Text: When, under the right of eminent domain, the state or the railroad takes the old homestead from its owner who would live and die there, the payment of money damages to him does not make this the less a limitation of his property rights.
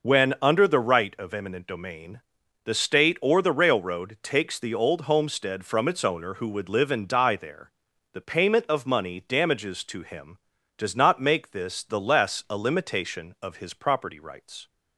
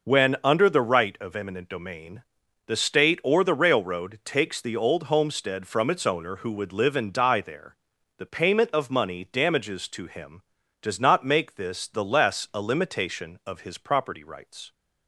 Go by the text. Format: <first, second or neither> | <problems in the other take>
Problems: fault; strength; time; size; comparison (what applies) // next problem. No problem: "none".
neither | none